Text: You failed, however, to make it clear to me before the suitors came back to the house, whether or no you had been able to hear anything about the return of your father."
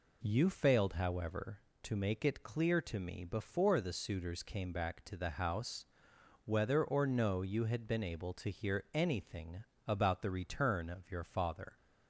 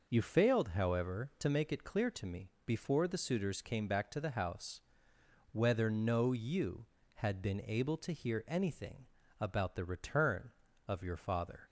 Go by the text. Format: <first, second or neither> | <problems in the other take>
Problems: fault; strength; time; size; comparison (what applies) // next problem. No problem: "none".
first | skips "or"; at 5.8 s // pauses between "anything" and "about"; slight; at 9.0 s; 0.34 s long; slight in the first